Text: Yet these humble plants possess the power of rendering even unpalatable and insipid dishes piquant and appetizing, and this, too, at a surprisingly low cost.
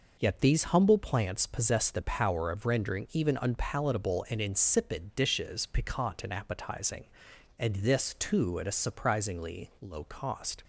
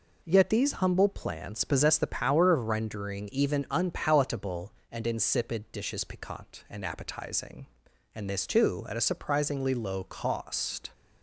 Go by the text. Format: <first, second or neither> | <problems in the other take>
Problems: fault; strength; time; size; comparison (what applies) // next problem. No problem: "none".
neither | none